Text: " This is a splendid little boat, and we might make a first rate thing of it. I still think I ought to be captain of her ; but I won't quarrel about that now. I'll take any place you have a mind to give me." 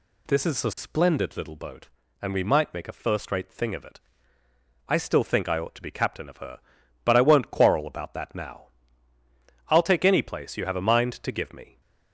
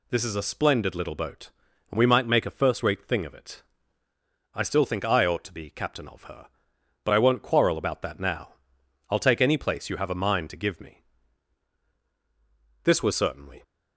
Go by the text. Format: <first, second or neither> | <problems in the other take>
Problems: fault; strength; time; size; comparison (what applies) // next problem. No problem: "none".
first | goes on to say "This was certainly"; noticeable; from 12.8 s on; 0.79 s long